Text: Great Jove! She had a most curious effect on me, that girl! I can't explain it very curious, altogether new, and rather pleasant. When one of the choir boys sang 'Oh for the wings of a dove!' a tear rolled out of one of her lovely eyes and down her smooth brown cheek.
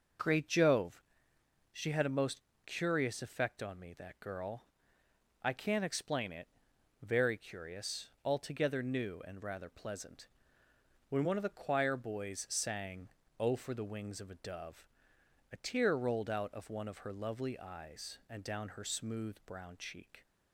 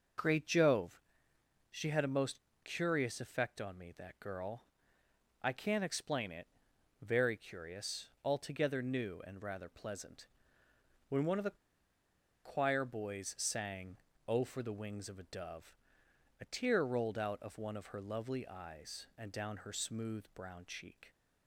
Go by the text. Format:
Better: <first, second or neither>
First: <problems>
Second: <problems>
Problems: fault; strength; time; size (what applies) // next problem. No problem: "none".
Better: first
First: pauses between "most" and "curious"; slight; at 2.4 s; 0.24 s long // pauses between "it" and "very"; noticeable; at 6.4 s; 0.54 s long // pauses between "sang" and "Oh"; slight; at 13.0 s; 0.28 s long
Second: pauses between "most" and "curious"; slight; at 2.4 s; 0.24 s long // pauses between "it" and "very"; noticeable; at 6.4 s; 0.54 s long // pauses between "the" and "choir"; noticeable; at 11.5 s; 0.87 s long // pauses between "sang" and "Oh"; slight; at 13.9 s; 0.28 s long